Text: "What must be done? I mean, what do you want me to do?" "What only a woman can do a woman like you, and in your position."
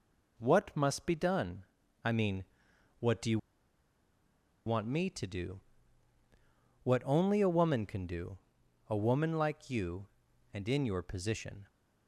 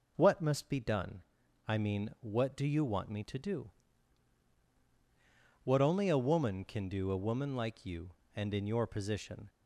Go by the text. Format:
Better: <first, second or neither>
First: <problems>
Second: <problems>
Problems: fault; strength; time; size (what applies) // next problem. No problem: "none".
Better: second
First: pauses between "you" and "want"; strong; at 3.3 s; 1.2 s long // pauses between "do" and "a"; noticeable; at 8.3 s; 0.52 s long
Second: none